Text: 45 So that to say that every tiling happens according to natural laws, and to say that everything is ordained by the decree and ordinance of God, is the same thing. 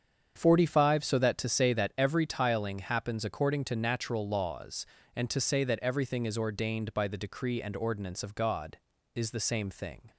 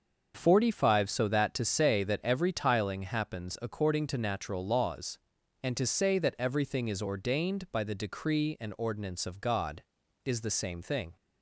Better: neither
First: starts louder than the rest; strong; until 1.3 s; 7.5 dB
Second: starts louder than the rest; until 1.3 s; 6.5 dB

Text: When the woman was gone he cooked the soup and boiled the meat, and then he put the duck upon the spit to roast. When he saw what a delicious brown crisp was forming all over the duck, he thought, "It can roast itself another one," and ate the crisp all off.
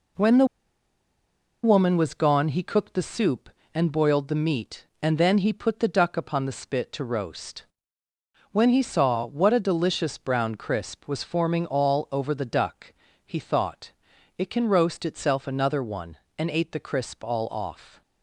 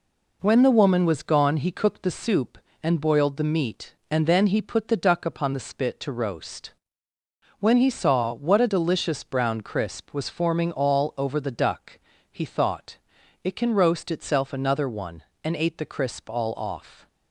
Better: second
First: pauses between "the" and "woman"; at 0.4 s; 1.1 s long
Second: none

